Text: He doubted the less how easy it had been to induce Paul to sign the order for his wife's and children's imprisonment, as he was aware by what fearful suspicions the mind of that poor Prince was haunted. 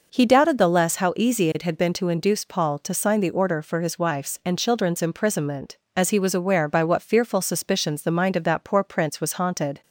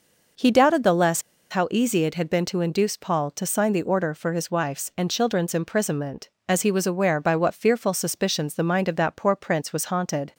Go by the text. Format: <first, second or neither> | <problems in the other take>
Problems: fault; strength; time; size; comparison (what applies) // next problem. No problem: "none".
first | pauses between "less" and "how"; slight; at 1.2 s; 0.29 s long